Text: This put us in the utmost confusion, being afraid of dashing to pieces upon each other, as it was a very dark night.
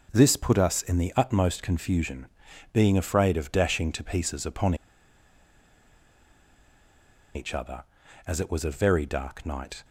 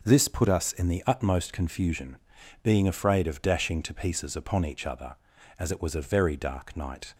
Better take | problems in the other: second | pauses between "upon" and "each"; strong; at 4.7 s; 2.6 s long

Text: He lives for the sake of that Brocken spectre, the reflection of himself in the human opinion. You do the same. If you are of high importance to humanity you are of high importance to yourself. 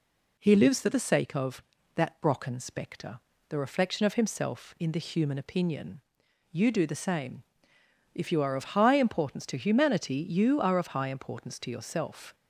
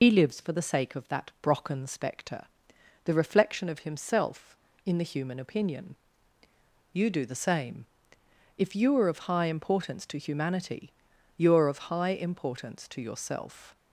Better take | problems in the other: first | loses the start of "He"; at 0.0 s; 65 ms // pauses between "humanity" and "you"; at 10.9 s; 0.44 s long

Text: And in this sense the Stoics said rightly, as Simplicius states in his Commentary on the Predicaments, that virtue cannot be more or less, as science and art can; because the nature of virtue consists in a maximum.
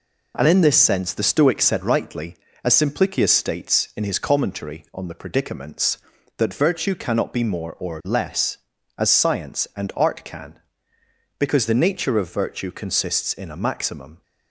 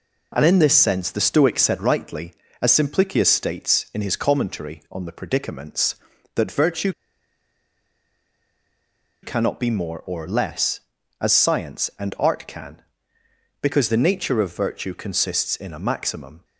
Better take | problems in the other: first | pauses between "virtue" and "cannot"; strong; at 6.9 s; 2.3 s long

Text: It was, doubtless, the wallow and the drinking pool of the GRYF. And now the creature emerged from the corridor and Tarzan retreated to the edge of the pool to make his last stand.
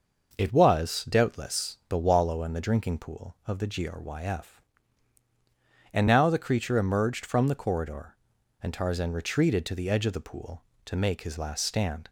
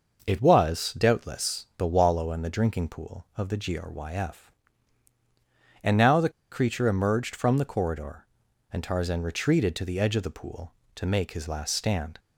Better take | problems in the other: first | pauses between "the" and "creature"; slight; at 6.2 s; 0.21 s long

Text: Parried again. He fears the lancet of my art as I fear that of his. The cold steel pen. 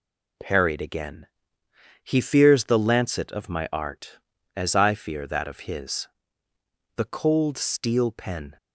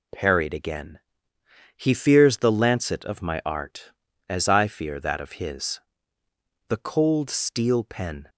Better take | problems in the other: neither | none

